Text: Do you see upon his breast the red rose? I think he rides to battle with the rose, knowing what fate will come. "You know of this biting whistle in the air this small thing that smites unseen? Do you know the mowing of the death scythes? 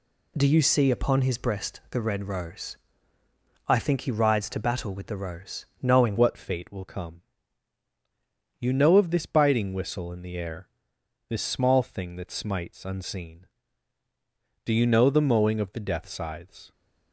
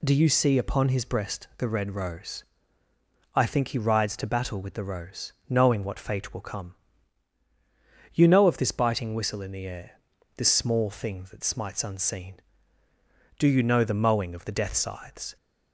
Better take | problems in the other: second | changes voice at "what"; from 6.1 s on; 10.6 s long // pauses between "air" and "this"; noticeable; at 10.6 s; 0.60 s long; also in the second

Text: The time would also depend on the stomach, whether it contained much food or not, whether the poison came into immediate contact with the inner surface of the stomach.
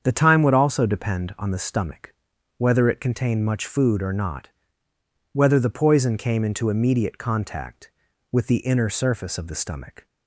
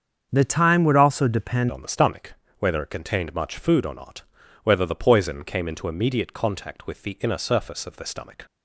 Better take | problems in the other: first | starts louder than the rest; strong; until 1.3 s; 7 dB; strong in the first // changes voice at "on"; from 1.6 s on; 6.8 s long

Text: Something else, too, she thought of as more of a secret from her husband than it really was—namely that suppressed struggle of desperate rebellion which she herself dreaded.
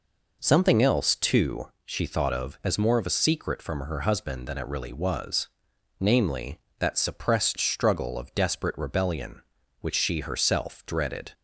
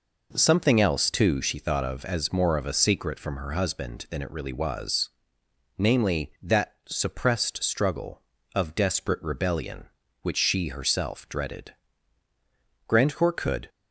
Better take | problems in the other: first | goes on to say "Grandcourt could"; noticeable; from 12.8 s on; 0.82 s long

